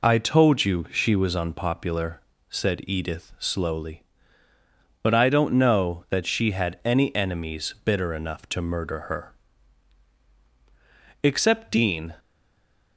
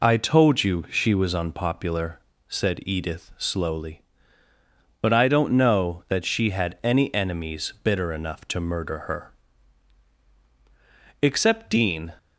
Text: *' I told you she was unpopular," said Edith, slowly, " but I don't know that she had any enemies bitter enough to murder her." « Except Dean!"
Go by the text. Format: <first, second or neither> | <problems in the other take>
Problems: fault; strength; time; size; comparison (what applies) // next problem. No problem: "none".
second | stays silent after the last word; slight; from 12.1 s on; 0.8 s long